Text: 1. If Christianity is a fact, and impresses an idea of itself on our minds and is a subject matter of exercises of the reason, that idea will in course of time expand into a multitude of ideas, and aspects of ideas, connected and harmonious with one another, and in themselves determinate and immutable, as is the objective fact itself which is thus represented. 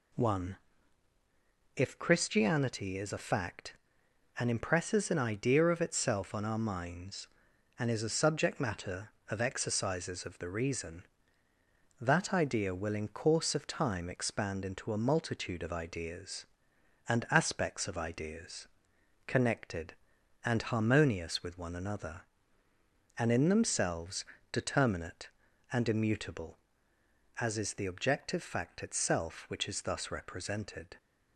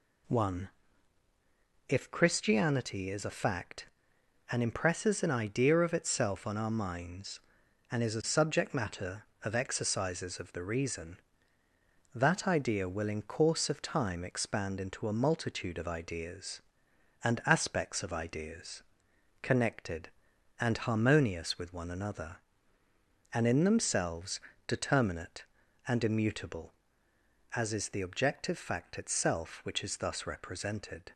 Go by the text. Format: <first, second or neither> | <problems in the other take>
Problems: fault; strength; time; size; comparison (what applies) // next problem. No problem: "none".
neither | pauses between "themselves" and "determinate"; slight; the same in both